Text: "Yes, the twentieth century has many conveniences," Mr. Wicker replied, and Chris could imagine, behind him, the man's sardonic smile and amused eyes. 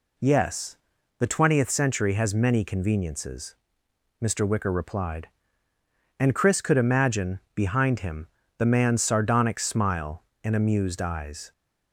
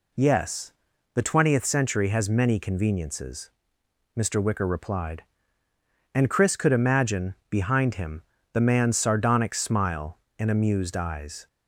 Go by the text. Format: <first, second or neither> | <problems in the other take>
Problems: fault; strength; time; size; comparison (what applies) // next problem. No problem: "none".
neither | none